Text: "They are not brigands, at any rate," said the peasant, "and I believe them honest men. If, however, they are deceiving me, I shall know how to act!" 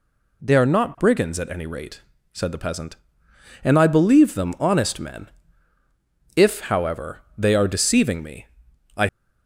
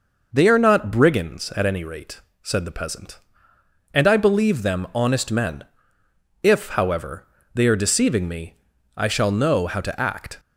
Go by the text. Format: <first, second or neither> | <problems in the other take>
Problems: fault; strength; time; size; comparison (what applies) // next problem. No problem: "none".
second | stops before "shall know how to act"; at 9.0 s